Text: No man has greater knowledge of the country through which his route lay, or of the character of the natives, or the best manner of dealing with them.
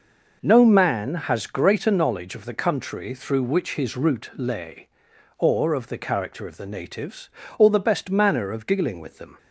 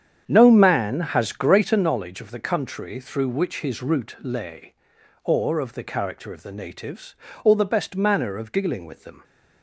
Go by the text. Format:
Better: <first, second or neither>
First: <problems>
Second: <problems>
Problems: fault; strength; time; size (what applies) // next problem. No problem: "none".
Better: first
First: none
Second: starts louder than the rest; strong; until 1.9 s; 8.5 dB